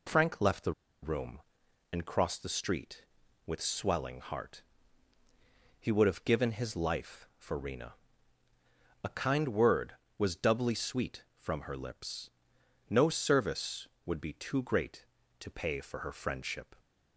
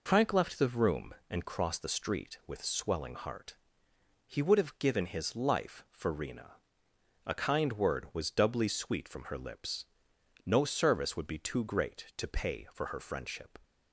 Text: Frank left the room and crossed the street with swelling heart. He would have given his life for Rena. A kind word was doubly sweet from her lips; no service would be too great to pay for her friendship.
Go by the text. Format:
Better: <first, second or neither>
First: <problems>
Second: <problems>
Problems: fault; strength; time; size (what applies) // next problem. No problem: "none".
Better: second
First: pauses between "the" and "room"; slight; at 0.7 s; 0.30 s long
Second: none